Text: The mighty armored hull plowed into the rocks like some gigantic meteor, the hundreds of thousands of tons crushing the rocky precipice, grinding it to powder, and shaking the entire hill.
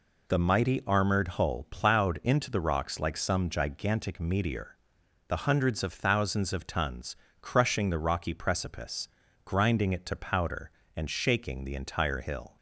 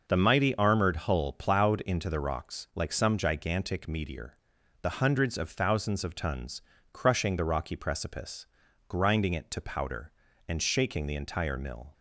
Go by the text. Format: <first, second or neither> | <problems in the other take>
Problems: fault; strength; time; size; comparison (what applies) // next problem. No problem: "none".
first | pauses between "tons" and "crushing"; slight; at 6.6 s; 0.32 s long; slight in the first // says "mill" for "hill"; at 11.5 s